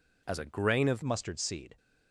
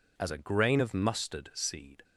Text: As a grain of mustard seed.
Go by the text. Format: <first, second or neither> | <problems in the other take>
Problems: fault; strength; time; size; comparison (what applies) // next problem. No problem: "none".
second | changes voice at "mustard"; from 1.0 s on; 0.7 s long